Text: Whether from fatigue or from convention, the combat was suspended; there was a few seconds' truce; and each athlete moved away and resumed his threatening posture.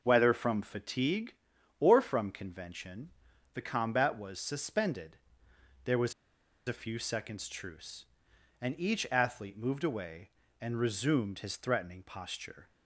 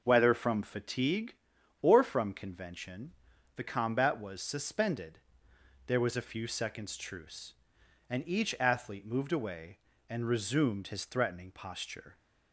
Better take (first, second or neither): second